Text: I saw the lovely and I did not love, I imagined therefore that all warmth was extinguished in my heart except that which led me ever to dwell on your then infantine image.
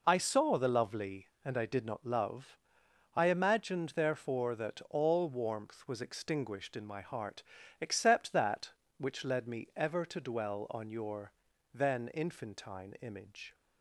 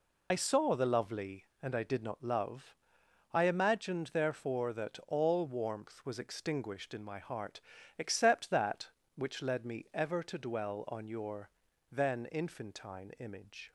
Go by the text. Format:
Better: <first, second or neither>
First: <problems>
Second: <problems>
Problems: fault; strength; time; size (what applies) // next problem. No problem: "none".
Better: first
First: pauses between "heart" and "except"; at 7.4 s; 0.40 s long // pauses between "your" and "then"; at 11.3 s; 0.42 s long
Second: loses the start of "I"; at 0.3 s; 65 ms // pauses between "heart" and "except"; at 7.5 s; 0.40 s long // pauses between "your" and "then"; at 11.4 s; 0.42 s long